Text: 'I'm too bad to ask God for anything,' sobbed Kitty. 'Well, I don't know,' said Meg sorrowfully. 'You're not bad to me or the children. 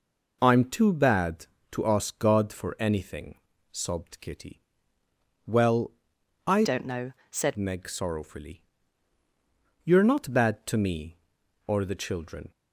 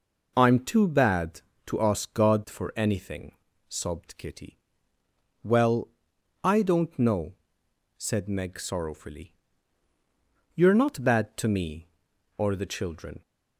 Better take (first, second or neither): second